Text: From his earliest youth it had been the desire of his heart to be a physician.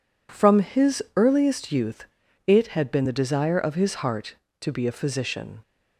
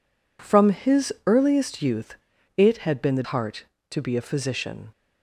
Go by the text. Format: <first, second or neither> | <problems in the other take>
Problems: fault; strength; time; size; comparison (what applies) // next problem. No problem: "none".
first | pauses between "youth" and "it"; at 2.1 s; 0.42 s long; also in the first // skips "desire of his"; at 3.2 s